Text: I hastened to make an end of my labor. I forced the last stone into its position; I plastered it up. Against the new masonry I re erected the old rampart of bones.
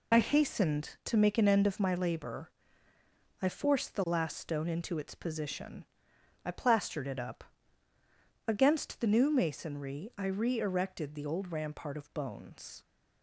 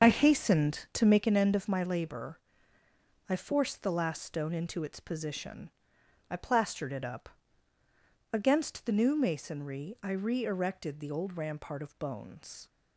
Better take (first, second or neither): first